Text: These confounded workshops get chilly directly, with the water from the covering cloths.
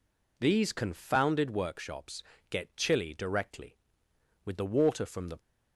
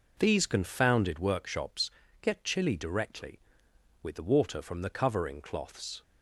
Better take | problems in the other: second | pauses between "workshops" and "get"; slight; at 2.2 s; 0.28 s long; slight in the second // stops before "covering cloths"; at 5.3 s

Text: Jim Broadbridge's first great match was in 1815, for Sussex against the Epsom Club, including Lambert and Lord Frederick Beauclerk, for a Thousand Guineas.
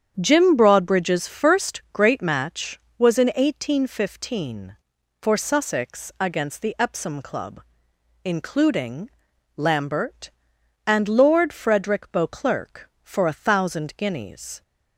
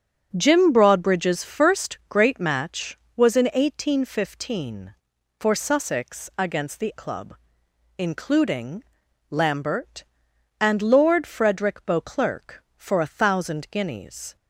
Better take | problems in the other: first | starts louder than the rest; strong; until 1.3 s; 8 dB; strong in the first // skips "Epsom"; at 6.9 s // pauses between "including" and "Lambert"; noticeable; at 8.8 s; 0.46 s long; noticeable in the first

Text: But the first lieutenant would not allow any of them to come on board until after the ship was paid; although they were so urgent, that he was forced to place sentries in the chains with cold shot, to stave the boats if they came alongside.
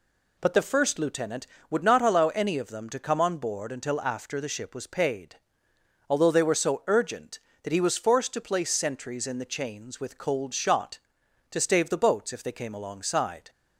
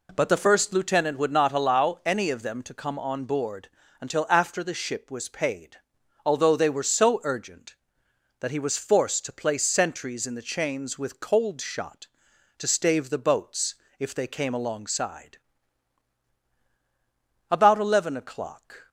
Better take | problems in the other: first | pauses between "board" and "until"; slight; at 3.6 s; 0.32 s long // pauses between "boats" and "if"; slight; at 13.7 s; 0.24 s long // goes on to say "About eleven o'clock"; from 17.5 s on; 1.3 s long

